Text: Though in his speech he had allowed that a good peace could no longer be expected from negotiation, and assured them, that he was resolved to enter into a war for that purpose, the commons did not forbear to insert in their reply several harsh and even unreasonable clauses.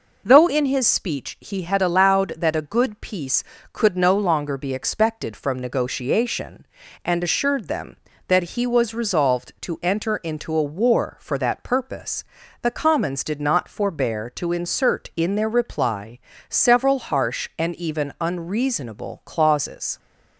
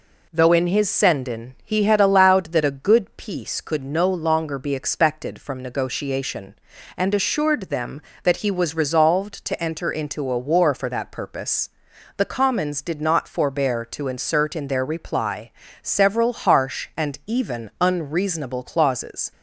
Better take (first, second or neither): first